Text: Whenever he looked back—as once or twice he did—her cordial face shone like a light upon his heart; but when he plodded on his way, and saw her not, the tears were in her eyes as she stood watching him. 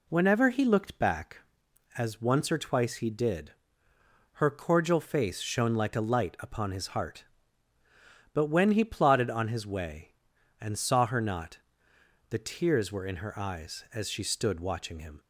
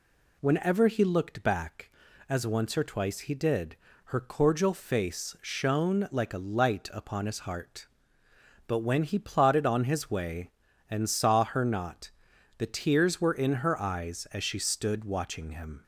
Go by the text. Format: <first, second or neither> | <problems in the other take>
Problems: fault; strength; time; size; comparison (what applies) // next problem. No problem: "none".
neither | none